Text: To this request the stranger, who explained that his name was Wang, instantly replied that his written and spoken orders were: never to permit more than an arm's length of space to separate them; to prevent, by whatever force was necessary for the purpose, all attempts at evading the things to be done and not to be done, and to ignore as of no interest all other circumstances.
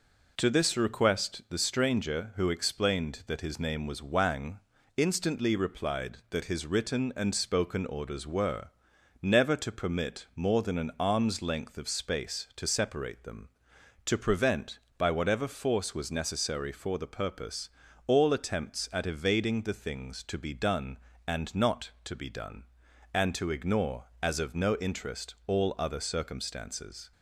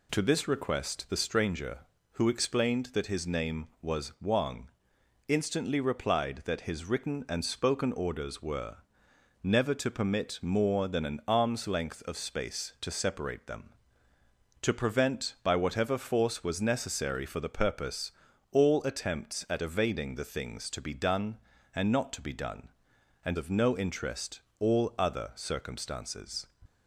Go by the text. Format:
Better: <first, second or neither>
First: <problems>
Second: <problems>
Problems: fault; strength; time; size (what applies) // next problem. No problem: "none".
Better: first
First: none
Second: skips "to ignore as"; at 23.3 s // pauses between "interest" and "all"; slight; at 24.4 s; 0.18 s long